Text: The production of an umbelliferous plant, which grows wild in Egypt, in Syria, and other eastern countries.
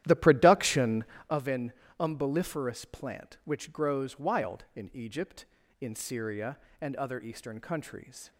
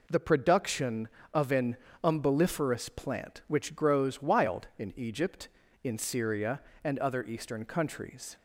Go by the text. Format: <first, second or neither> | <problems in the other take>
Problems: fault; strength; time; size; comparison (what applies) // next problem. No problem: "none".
second | starts louder than the rest; strong; until 1.4 s; 12.5 dB // pauses between "an" and "umbelliferous"; slight; at 1.7 s; 0.26 s long; slight in the second